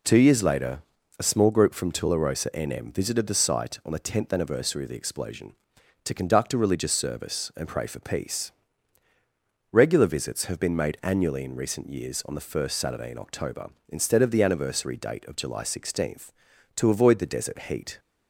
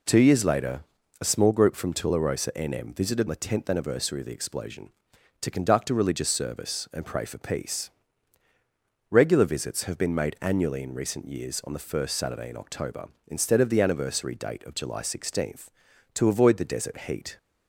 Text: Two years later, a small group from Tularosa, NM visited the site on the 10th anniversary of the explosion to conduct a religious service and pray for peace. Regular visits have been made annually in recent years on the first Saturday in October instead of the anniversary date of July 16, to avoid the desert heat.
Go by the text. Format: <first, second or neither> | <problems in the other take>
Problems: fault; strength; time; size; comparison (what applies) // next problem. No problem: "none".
first | skips "the site on"; at 3.2 s